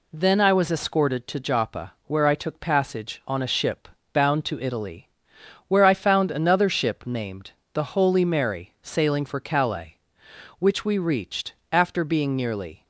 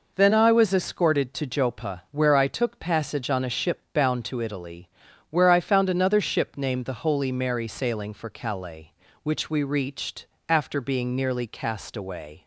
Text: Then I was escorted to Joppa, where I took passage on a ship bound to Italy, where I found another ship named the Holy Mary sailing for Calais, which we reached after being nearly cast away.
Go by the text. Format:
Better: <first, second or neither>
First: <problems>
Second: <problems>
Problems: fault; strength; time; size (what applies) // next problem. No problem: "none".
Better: second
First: pauses between "ship" and "bound"; slight; at 3.8 s; 0.24 s long // pauses between "named" and "the"; slight; at 7.5 s; 0.22 s long // pauses between "reached" and "after"; slight; at 11.5 s; 0.20 s long // stops before "cast away"; at 12.8 s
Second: pauses between "reached" and "after"; slight; at 10.2 s; 0.24 s long